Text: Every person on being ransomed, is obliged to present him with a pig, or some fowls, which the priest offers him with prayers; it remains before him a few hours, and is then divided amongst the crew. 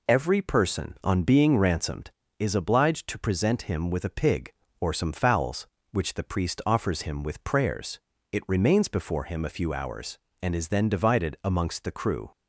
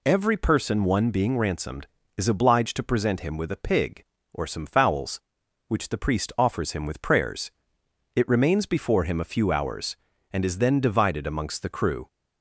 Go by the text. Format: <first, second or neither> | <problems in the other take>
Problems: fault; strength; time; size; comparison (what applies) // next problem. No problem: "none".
first | says "one" for "on"; at 0.8 s